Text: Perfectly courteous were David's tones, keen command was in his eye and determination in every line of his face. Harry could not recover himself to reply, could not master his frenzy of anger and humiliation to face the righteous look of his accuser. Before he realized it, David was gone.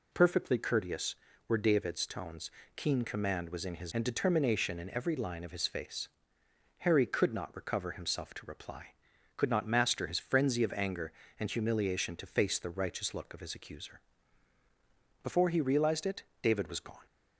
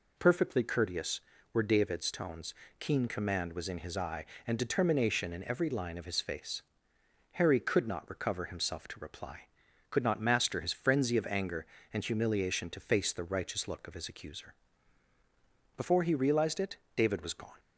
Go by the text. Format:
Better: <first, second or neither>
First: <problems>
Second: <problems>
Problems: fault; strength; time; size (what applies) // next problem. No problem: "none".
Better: second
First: skips "eye"; at 3.9 s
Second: none